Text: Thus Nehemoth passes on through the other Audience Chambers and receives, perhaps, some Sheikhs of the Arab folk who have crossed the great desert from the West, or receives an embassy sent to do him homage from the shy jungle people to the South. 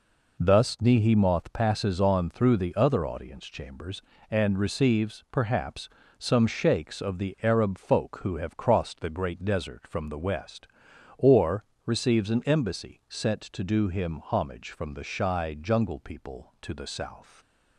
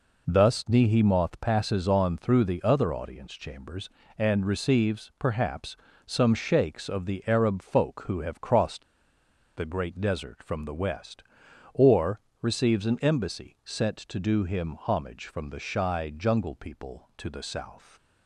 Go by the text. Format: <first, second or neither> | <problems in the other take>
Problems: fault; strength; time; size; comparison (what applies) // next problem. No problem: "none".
first | pauses between "crossed" and "the"; noticeable; at 8.8 s; 0.71 s long // pauses between "or" and "receives"; slight; at 12.1 s; 0.22 s long; slight in the first